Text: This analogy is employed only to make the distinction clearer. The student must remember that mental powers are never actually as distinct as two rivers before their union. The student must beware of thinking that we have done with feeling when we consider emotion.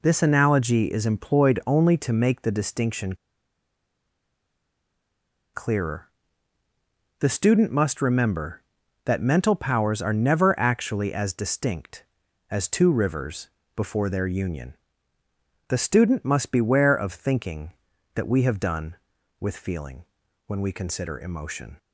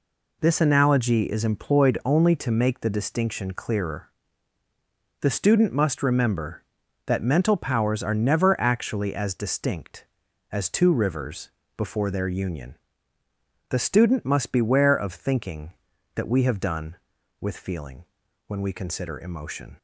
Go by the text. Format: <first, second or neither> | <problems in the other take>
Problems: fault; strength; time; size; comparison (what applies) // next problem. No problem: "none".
second | pauses between "distinction" and "clearer"; strong; at 3.1 s; 2.3 s long // pauses between "rivers" and "before"; slight; at 13.4 s; 0.26 s long; slight in the second // pauses between "feeling" and "when"; at 20.0 s; 0.42 s long; also in the second